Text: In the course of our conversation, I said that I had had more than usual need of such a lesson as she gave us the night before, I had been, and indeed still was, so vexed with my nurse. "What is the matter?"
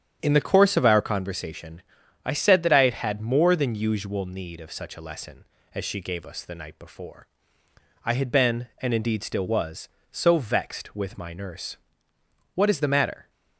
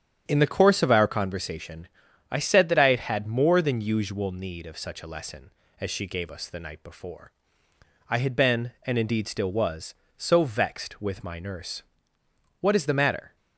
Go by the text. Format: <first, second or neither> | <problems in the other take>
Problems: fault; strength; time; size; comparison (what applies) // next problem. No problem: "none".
neither | starts louder than the rest; strong; the same in both